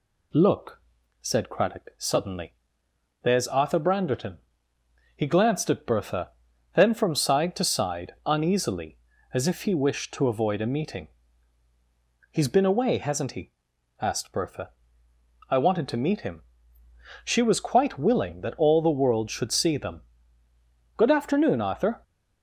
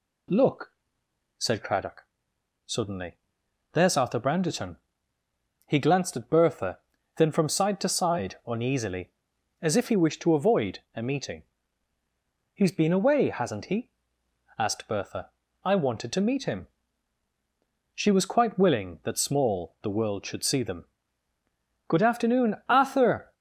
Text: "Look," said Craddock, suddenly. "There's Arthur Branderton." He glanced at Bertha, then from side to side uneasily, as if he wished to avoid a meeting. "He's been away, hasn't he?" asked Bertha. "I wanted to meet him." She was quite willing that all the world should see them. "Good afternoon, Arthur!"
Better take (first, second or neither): first